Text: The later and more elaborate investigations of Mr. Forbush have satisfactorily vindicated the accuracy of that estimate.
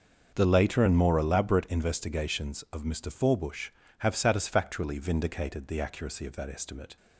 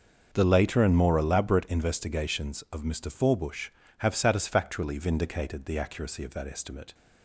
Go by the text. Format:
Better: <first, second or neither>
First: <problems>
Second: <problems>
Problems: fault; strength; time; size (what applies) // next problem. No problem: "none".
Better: neither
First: starts louder than the rest; until 1.3 s; 6.5 dB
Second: starts louder than the rest; until 1.3 s; 6 dB